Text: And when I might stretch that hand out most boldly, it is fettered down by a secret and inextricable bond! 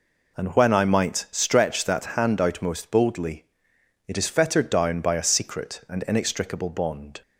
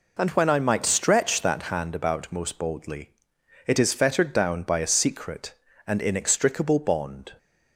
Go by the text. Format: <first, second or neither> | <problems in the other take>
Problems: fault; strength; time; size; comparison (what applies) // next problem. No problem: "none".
first | says "about" for "out"; at 1.9 s